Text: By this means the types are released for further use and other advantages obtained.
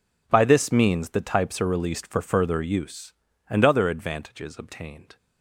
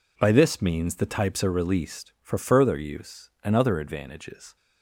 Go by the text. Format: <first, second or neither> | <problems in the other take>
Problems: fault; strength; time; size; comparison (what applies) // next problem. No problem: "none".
first | stops before "obtained"; at 4.5 s